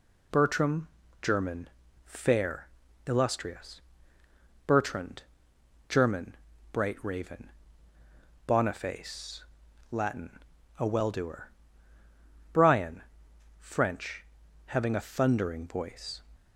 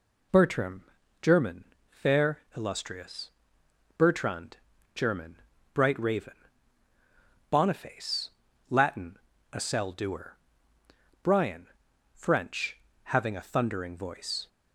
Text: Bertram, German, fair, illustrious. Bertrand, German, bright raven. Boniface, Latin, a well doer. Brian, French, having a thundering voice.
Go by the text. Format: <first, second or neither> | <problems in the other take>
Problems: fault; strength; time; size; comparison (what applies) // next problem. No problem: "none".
first | says "cell" for "well"; at 9.5 s